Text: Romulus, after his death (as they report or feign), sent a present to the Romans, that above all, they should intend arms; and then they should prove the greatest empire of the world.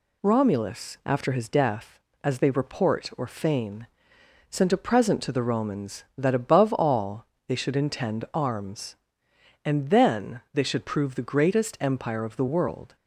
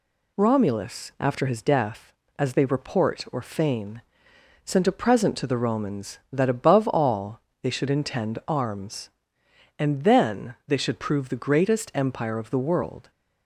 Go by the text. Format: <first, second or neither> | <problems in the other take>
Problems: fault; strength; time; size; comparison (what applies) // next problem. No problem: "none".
neither | none